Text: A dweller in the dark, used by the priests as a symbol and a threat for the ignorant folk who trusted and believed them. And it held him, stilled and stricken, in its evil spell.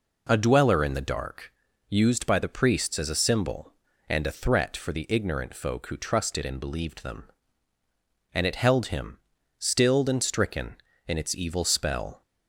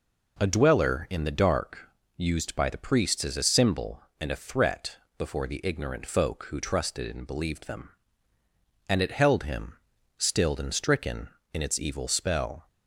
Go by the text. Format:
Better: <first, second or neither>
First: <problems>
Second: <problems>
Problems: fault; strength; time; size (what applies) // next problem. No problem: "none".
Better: first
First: none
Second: says "before" for "for"; at 5.1 s